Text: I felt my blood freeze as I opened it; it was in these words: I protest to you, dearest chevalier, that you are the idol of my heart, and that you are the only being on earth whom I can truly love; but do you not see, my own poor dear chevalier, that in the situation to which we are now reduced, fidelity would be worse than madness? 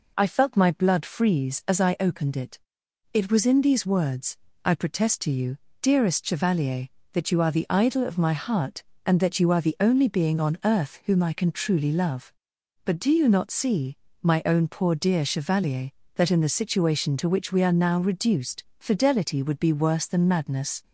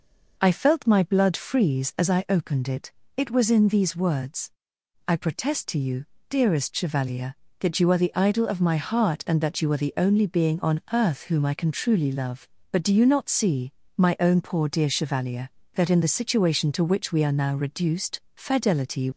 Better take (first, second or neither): first